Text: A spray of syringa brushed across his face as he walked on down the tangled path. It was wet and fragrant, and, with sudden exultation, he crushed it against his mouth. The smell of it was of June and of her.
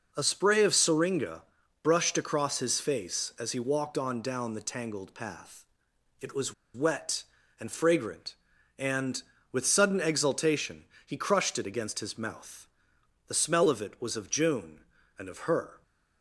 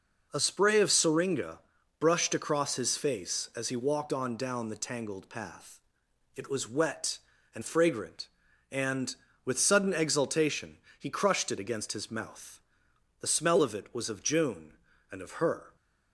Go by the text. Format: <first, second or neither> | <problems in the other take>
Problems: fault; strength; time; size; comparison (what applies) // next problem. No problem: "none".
second | pauses between "syringa" and "brushed"; at 1.4 s; 0.42 s long; also in the second // pauses between "was" and "wet"; slight; at 6.5 s; 0.22 s long